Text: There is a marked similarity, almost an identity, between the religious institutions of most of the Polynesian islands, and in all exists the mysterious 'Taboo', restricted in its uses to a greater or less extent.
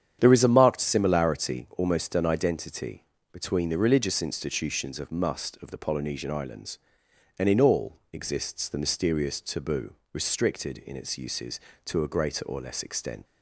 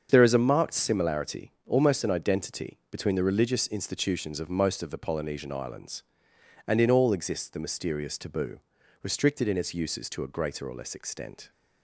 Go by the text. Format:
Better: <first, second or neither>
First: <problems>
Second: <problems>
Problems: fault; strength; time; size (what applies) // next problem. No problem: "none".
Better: second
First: starts louder than the rest; strong; until 1.2 s; 9 dB // says "must" for "most"; at 5.0 s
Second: starts louder than the rest; until 1.1 s; 7 dB